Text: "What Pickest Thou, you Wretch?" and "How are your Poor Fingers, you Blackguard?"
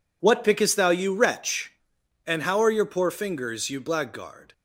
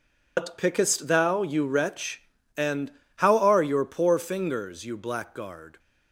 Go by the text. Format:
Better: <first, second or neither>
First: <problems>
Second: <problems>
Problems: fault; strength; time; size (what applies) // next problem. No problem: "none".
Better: first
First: none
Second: loses the start of "What"; at 0.3 s; 105 ms // pauses between "and" and "How"; slight; at 2.9 s; 0.23 s long